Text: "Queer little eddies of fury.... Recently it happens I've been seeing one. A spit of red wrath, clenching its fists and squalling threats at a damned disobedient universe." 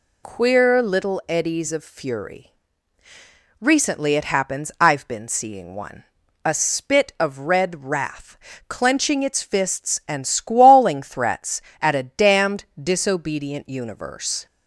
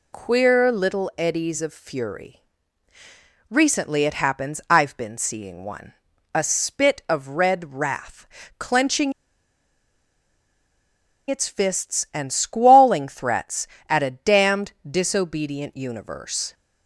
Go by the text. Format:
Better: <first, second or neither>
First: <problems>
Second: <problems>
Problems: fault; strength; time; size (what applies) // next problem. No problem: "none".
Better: first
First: none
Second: pauses between "clenching" and "its"; strong; at 9.1 s; 2.1 s long